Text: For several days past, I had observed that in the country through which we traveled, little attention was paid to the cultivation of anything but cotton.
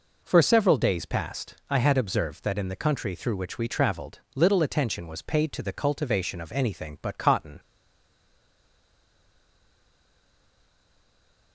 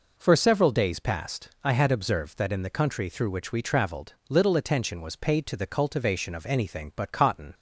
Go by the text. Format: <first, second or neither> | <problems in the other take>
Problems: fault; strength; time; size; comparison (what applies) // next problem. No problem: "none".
second | stays silent after the last word; strong; from 7.5 s on; 4.0 s long